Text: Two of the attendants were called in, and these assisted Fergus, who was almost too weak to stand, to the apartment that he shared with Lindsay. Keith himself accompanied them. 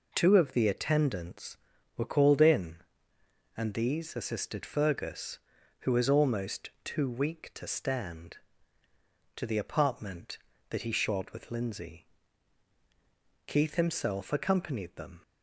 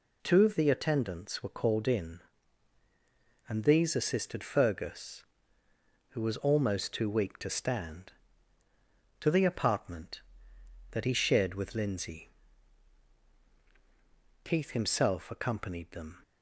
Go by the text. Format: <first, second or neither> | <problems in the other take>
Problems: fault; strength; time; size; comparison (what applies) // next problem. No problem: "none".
neither | none